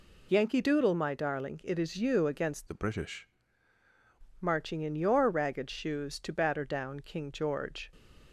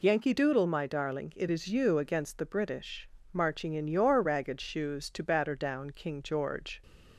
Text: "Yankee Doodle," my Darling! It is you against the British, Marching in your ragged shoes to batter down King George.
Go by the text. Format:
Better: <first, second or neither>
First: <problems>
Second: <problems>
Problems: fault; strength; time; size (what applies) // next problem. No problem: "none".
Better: second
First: changes voice from "the" to "British"; from 2.6 to 3.2 s; 0.6 s long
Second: none